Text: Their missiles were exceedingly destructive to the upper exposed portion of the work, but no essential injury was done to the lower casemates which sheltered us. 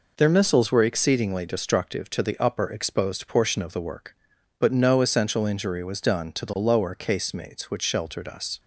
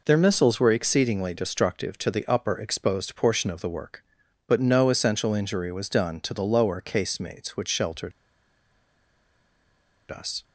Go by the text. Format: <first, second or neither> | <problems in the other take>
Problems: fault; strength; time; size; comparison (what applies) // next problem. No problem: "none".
first | pauses between "sheltered" and "us"; strong; at 8.1 s; 1.9 s long